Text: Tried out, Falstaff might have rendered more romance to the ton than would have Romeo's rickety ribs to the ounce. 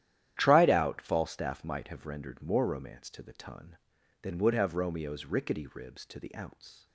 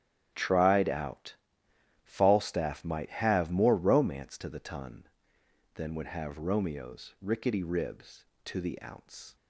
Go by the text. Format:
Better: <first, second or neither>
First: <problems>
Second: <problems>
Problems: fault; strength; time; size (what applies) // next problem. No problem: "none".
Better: first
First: starts louder than the rest; strong; until 1.3 s; 11 dB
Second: starts louder than the rest; strong; until 1.3 s; 11.5 dB // skips "rendered"; at 3.5 s